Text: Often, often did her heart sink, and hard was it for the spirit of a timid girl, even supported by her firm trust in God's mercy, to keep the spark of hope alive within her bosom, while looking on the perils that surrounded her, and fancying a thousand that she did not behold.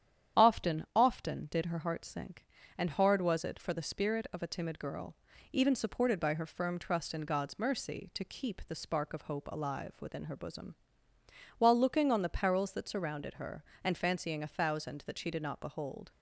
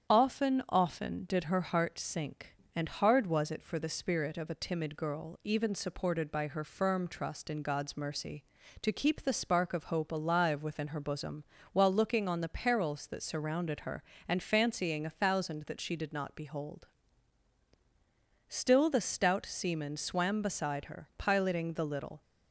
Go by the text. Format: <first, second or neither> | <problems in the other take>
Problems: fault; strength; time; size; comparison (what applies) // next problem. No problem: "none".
first | starts louder than the rest; strong; until 1.1 s; 8.5 dB; strong in the first // goes on to say "Still the stout seaman swam beside her piloting the little"; strong; from 18.4 s on; 3.7 s long